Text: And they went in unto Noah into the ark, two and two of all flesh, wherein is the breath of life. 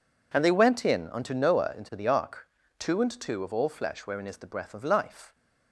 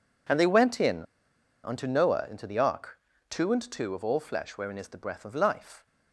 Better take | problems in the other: first | pauses between "in" and "unto"; noticeable; at 1.0 s; 0.60 s long

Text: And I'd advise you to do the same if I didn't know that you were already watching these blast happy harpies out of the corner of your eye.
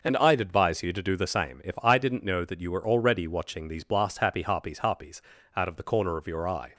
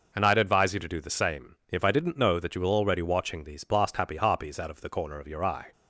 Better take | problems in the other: second | says "harpies" twice; at 4.7 s

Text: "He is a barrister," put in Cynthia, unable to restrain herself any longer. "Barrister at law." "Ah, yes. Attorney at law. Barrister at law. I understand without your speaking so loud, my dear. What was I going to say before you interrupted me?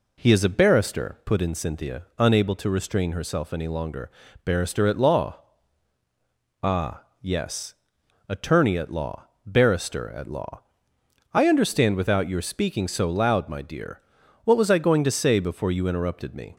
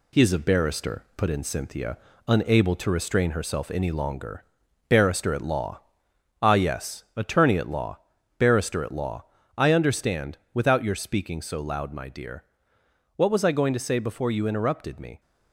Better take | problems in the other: first | gets quieter; throughout; 3.5 dB // pauses between "understand" and "without"; slight; at 10.3 s; 0.16 s long

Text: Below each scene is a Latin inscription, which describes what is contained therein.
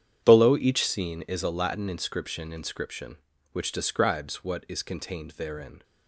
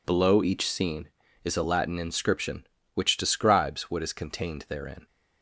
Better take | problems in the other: second | starts louder than the rest; strong; until 1.2 s; 8.5 dB // says "inscription" twice; at 2.5 s

